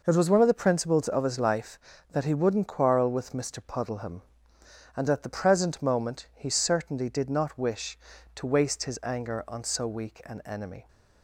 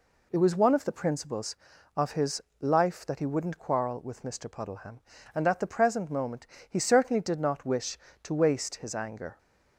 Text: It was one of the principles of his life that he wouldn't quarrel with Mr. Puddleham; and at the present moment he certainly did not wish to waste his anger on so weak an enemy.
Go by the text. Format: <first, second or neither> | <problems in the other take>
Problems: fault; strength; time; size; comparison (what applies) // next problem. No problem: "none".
first | pauses between "his" and "life"; slight; at 2.4 s; 0.20 s long // pauses between "moment" and "he"; slight; at 6.4 s; 0.20 s long // stops before "on so weak an enemy"; at 9.3 s